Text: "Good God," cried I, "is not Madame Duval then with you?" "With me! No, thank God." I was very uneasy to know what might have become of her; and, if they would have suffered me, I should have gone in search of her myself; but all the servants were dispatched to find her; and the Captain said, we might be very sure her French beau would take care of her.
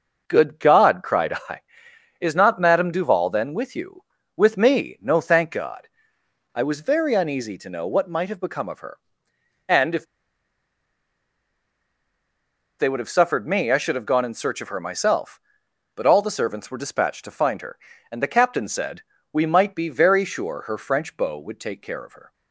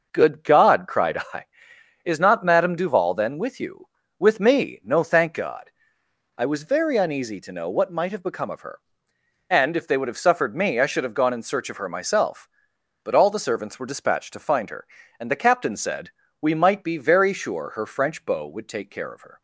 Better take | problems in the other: second | pauses between "if" and "they"; strong; at 10.0 s; 2.7 s long

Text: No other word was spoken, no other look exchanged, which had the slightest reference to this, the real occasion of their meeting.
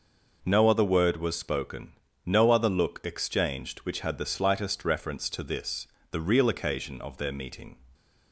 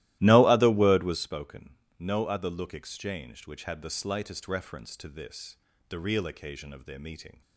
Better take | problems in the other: first | starts louder than the rest; strong; until 1.3 s; 15.5 dB

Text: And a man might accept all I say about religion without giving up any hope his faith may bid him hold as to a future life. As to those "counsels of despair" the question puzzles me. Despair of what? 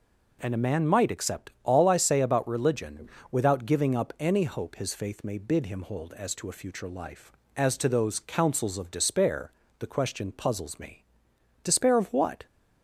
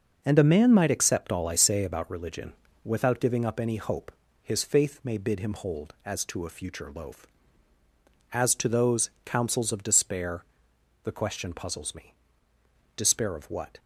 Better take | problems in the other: first | pauses between "religion" and "without"; slight; at 2.5 s; 0.32 s long; slight in the first // pauses between "hope" and "his"; slight; at 4.1 s; 0.28 s long // says "loaf" for "life"; at 6.9 s // pauses between "despair" and "the"; noticeable; at 10.4 s; 0.58 s long; slight in the first

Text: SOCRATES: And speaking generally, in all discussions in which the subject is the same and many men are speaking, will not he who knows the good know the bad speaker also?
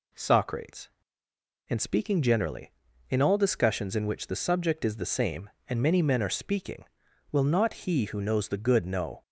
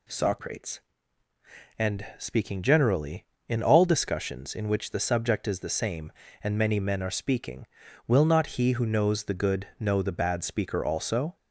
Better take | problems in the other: second | stops before "the bad speaker also"; at 9.2 s

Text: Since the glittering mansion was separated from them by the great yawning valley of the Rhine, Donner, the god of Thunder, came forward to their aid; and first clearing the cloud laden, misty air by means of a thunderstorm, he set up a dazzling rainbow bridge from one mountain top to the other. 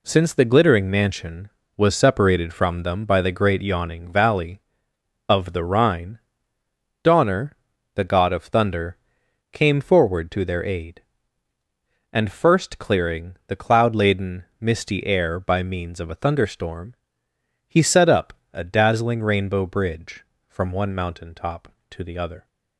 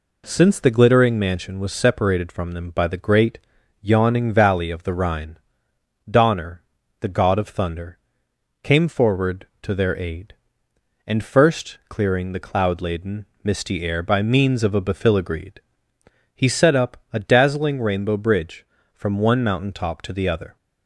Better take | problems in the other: first | pauses between "great" and "yawning"; noticeable; at 3.3 s; 0.46 s long // says "befiligreed" for "thunderstorm"; at 14.8 s // pauses between "up" and "a"; slight; at 16.9 s; 0.16 s long; slight in the first

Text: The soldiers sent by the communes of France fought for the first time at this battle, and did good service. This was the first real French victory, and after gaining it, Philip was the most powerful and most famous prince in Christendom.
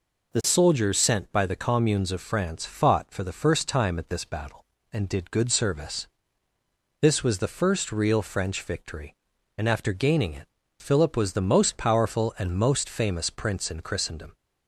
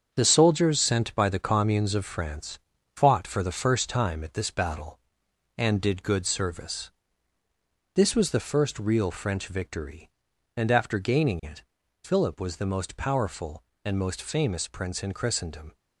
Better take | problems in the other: first | gets quieter; strong; throughout; 8 dB // pauses between "France" and "fought"; slight; at 2.5 s; 0.36 s long

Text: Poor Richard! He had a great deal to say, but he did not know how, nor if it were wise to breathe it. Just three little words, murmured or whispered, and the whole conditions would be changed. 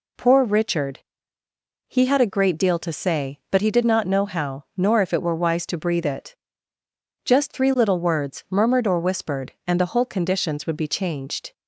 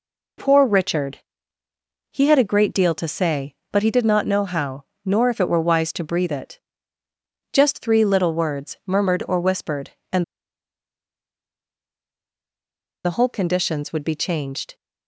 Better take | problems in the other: first | pauses between "and" and "the"; strong; at 10.2 s; 2.8 s long

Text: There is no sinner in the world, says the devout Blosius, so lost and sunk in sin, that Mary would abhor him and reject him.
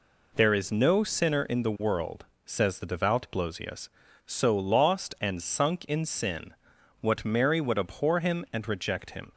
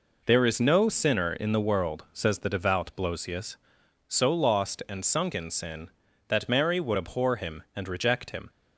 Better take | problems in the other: second | says "what" for "that"; at 7.0 s

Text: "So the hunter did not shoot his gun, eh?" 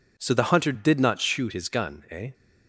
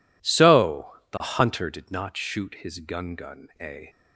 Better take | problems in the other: first | says "gun" twice; at 3.1 s

